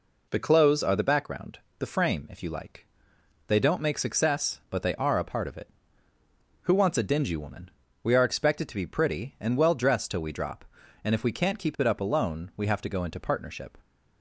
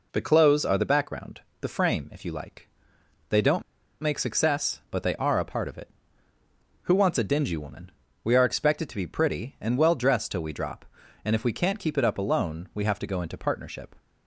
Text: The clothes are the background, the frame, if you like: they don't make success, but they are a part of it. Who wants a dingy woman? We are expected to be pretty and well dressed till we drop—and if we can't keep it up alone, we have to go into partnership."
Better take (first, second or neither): first